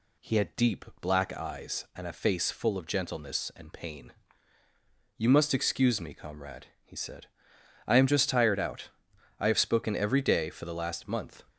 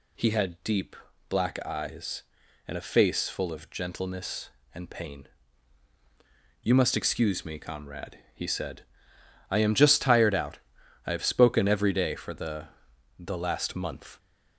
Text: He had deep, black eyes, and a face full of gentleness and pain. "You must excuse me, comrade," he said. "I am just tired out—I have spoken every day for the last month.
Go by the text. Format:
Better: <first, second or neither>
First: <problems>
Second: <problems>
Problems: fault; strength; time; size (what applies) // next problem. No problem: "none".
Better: first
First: none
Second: says "the" twice; at 13.1 s